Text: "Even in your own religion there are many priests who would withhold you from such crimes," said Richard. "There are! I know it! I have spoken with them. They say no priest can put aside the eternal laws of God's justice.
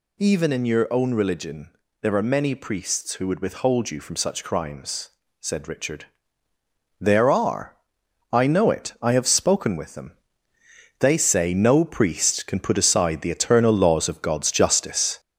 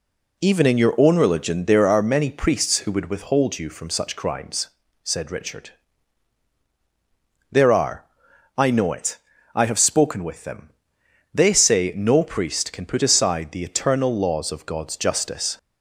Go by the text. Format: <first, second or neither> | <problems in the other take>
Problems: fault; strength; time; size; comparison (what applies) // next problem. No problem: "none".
second | gets louder; noticeable; throughout; 4.5 dB // pauses between "religion" and "there"; slight; at 1.6 s; 0.32 s long